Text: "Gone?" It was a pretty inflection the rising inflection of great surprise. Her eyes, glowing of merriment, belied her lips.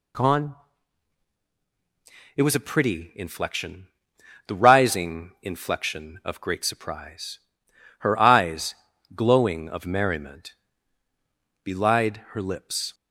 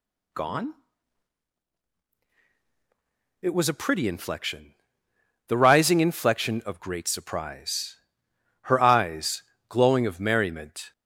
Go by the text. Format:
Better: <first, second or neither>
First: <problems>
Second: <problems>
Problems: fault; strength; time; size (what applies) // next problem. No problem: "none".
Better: first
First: pauses between "inflection" and "the"; noticeable; at 3.8 s; 0.58 s long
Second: pauses between "inflection" and "the"; noticeable; at 4.7 s; 0.72 s long // stops before "belied her lips"; at 10.9 s